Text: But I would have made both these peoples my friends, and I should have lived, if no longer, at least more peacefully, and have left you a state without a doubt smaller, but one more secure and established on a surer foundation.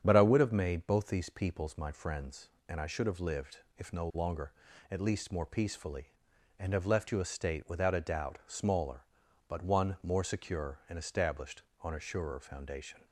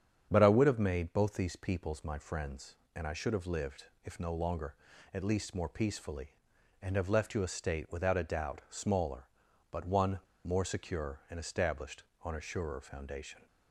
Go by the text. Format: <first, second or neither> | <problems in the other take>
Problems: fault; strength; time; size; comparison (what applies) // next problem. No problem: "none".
first | starts louder than the rest; strong; until 1.3 s; 8 dB; strong in the first // pauses between "one" and "more"; slight; at 10.2 s; 0.24 s long